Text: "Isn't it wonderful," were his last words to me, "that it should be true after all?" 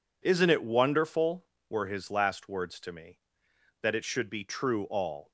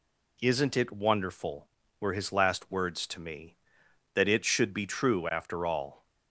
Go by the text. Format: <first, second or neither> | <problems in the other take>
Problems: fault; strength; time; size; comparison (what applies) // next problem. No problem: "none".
second | skips "after"; at 4.8 s